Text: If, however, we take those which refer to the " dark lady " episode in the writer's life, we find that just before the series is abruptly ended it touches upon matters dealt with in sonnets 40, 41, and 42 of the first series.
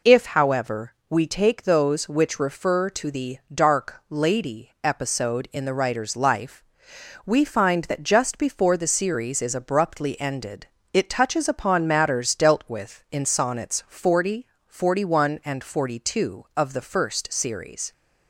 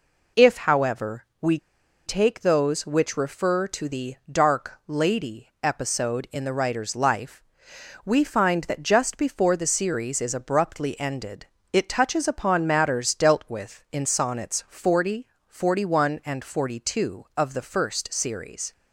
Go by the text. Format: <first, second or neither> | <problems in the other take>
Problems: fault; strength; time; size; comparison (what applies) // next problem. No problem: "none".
first | pauses between "we" and "take"; noticeable; at 1.5 s; 0.47 s long // pauses between "ended" and "it"; slight; at 11.4 s; 0.26 s long; slight in the first